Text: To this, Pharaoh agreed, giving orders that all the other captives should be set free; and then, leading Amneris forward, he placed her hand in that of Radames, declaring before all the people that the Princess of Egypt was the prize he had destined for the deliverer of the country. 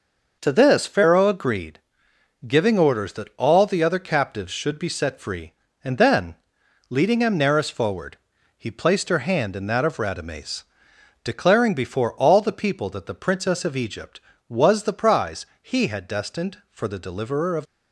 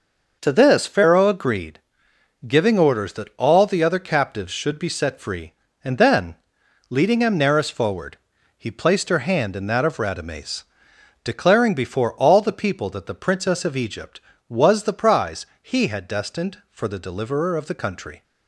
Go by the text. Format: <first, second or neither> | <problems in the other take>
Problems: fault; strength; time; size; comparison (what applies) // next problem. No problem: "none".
second | pauses between "prize" and "he"; slight; at 15.4 s; 0.16 s long; slight in the second // stops before "the country"; at 17.6 s